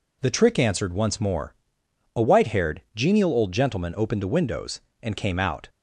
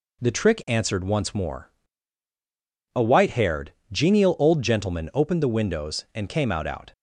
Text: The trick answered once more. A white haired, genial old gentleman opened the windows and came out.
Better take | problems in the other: first | says "out" twice; at 6.6 s

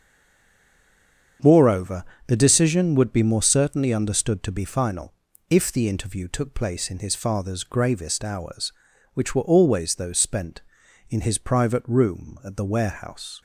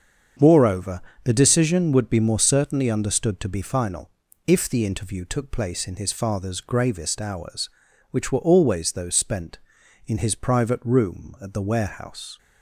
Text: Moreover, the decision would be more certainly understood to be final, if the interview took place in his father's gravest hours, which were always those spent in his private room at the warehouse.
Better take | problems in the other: second | stays silent before the first word; noticeable; until 1.3 s; 1.3 s long // starts louder than the rest; strong; until 2.6 s; 7 dB; strong in the second

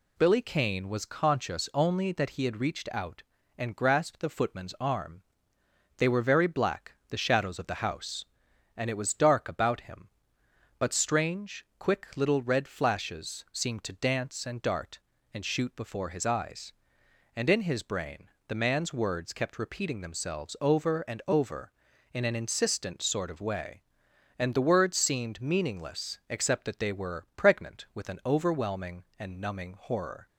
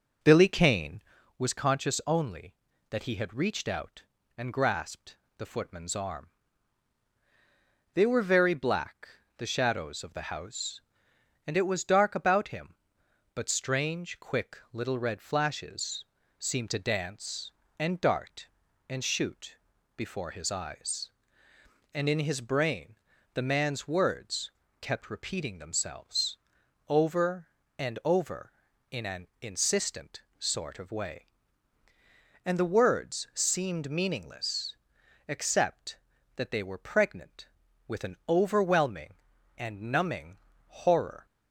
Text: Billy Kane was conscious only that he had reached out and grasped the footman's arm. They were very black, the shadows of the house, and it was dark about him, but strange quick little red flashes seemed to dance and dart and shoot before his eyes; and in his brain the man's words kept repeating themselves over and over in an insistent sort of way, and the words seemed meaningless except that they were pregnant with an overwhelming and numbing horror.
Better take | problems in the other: first | starts louder than the rest; noticeable; until 1.2 s; 4.5 dB // pauses between "grasped" and "the"; slight; at 5.1 s; 0.20 s long // pauses between "flashes" and "seemed"; slight; at 16.0 s; 0.32 s long // pauses between "shoot" and "before"; at 19.5 s; 0.42 s long // pauses between "brain" and "the"; at 22.9 s; 0.38 s long; slight in the first // pauses between "words" and "kept"; slight; at 24.5 s; 0.30 s long // pauses between "themselves" and "over"; noticeable; at 26.3 s; 0.50 s long // pauses between "an" and "insistent"; slight; at 29.2 s; 0.16 s long // pauses between "insistent" and "sort"; slight; at 30.2 s; 0.16 s long // pauses between "meaningless" and "except"; noticeable; at 34.7 s; 0.52 s long // pauses between "numbing" and "horror"; slight; at 40.3 s; 0.30 s long

